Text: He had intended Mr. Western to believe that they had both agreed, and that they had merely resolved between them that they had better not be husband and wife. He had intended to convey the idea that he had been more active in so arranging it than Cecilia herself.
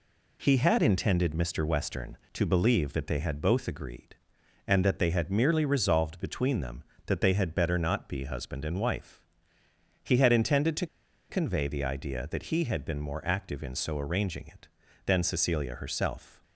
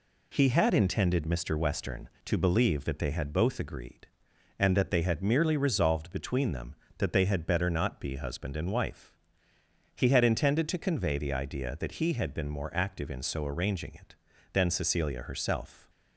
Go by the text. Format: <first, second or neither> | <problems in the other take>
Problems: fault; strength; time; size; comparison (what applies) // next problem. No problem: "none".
second | pauses between "to" and "convey"; at 10.8 s; 0.42 s long